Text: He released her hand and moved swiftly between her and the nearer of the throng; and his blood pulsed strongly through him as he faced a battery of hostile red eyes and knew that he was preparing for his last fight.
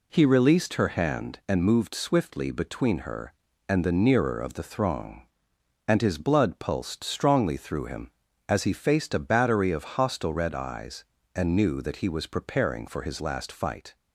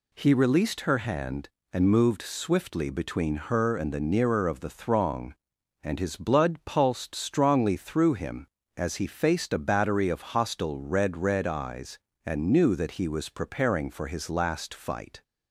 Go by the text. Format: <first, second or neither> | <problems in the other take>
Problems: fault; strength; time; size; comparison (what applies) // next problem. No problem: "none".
first | says "red" twice; at 11.1 s